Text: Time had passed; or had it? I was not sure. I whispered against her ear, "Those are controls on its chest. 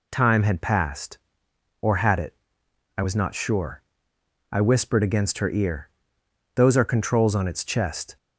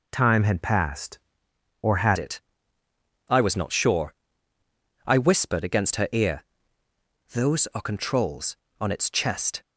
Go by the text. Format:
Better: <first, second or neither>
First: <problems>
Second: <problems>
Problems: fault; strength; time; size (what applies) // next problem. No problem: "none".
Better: first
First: none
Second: changes voice at "it"; from 2.1 s on; 7.5 s long